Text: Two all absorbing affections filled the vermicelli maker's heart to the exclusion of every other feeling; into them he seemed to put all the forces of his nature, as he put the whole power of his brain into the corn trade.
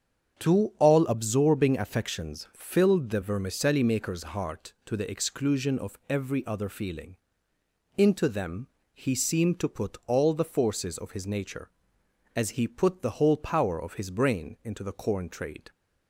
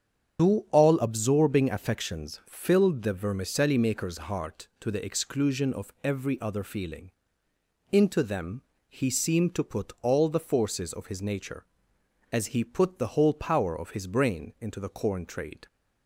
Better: first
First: starts louder than the rest; strong; until 1.4 s; 7.5 dB // pauses between "them" and "he"; slight; at 8.6 s; 0.25 s long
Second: loses the start of "Two"; at 0.3 s; 85 ms // starts louder than the rest; strong; until 1.4 s; 8 dB // pauses between "them" and "he"; slight; at 8.6 s; 0.26 s long

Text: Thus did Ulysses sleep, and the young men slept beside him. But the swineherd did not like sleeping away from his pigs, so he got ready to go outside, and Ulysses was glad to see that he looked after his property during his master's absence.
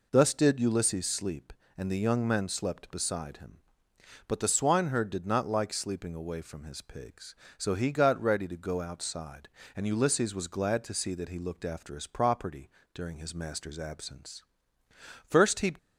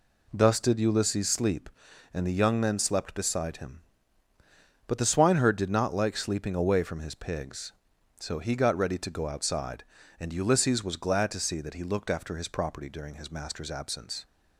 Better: second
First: pauses between "property" and "during"; slight; at 12.6 s; 0.24 s long // goes on to say "First he"; from 15.2 s on; 0.50 s long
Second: none

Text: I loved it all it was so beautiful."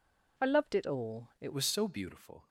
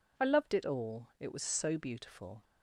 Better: second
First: changes voice at "was"; from 1.5 s on; 0.9 s long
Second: none

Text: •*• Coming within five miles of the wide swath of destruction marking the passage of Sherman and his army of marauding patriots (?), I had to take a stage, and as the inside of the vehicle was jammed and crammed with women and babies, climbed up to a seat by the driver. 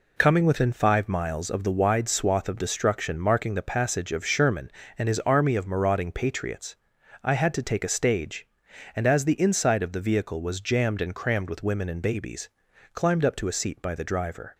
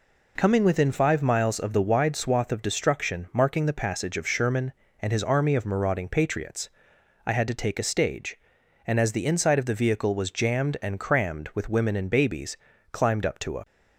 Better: first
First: none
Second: stops before "seat by the driver"; at 13.6 s

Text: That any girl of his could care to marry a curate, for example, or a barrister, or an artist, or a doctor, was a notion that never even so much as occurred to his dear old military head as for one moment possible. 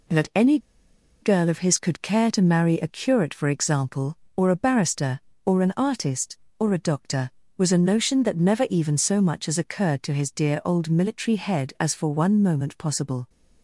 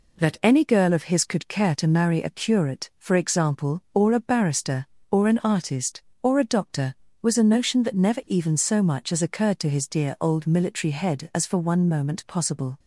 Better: second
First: pauses between "any" and "girl"; noticeable; at 0.5 s; 0.64 s long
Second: none

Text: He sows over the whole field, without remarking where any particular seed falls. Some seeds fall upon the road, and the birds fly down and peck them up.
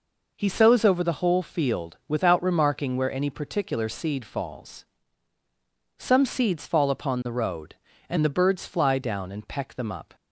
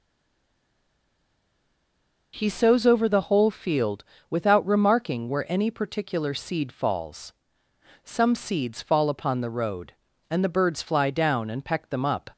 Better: first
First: none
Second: stays silent before the first word; until 2.3 s; 2.3 s long

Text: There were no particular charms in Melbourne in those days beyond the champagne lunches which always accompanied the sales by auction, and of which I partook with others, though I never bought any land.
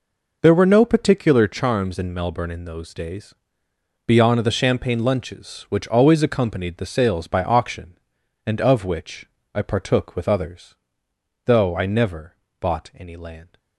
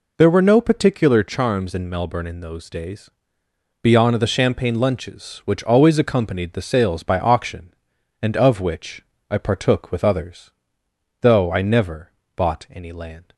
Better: second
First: gets quieter; strong; throughout; 11.5 dB // pauses between "days" and "beyond"; noticeable; at 3.3 s; 0.72 s long // pauses between "which" and "I"; slight; at 9.2 s; 0.26 s long // pauses between "never" and "bought"; slight; at 12.3 s; 0.26 s long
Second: pauses between "days" and "beyond"; noticeable; at 3.0 s; 0.72 s long // pauses between "which" and "I"; slight; at 9.0 s; 0.26 s long // pauses between "never" and "bought"; slight; at 12.0 s; 0.26 s long

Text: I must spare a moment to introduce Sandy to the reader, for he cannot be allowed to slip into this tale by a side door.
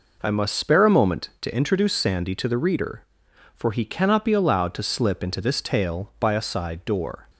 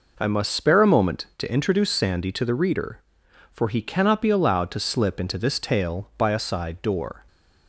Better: neither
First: none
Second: none

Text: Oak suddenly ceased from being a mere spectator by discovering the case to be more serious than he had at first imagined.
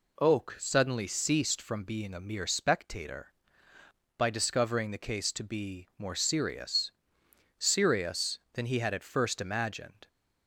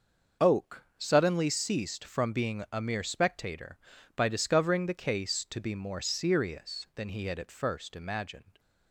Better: second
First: says "serious" twice; at 7.5 s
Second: none

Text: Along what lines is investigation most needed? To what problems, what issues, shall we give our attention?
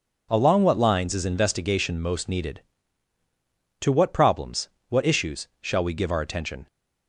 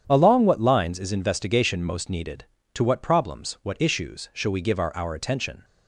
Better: first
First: none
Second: starts louder than the rest; strong; until 1.0 s; 9 dB // says "our" twice; at 4.9 s

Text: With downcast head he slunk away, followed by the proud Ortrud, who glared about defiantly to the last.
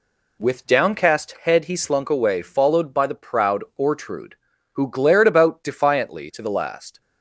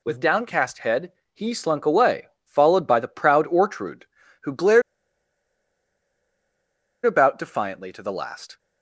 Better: first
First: none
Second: pauses between "head" and "he"; slight; at 1.1 s; 0.20 s long // pauses between "glared" and "about"; strong; at 4.8 s; 2.2 s long

